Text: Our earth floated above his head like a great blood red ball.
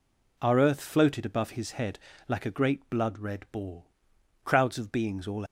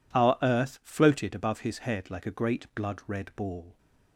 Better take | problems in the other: second | pauses between "head" and "like"; slight; at 1.9 s; 0.30 s long // goes on to say "Crowds of beings all"; noticeable; from 4.4 s on; 1.0 s long

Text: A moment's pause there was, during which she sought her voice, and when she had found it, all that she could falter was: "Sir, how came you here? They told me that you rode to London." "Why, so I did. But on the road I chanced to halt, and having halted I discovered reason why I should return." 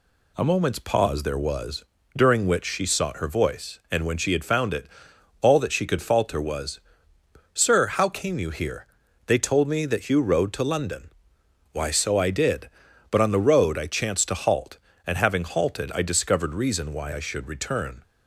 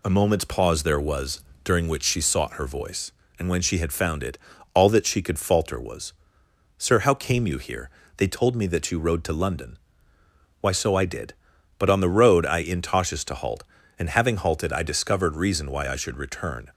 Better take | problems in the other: first | says "intoshes" for "chanced"; at 12.6 s

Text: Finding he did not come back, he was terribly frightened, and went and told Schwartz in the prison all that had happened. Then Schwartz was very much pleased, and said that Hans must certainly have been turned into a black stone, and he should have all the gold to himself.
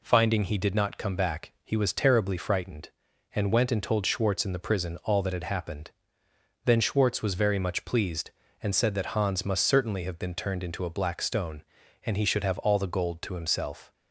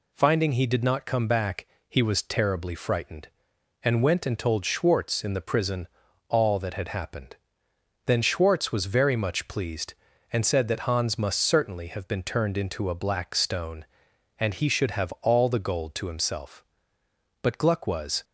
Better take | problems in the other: first | pauses between "prison" and "all"; at 5.8 s; 0.40 s long // goes on to say "But Gluck was"; noticeable; from 17.4 s on; 0.82 s long

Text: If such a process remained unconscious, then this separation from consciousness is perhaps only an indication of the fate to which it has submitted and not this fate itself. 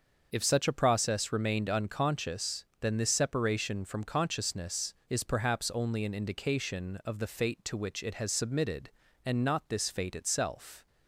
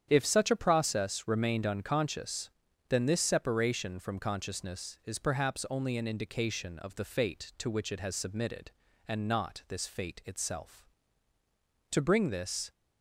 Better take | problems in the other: first | starts louder than the rest; strong; until 1.1 s; 9 dB; also in the first // goes on to say "To bring this"; noticeable; from 11.9 s on; 0.80 s long

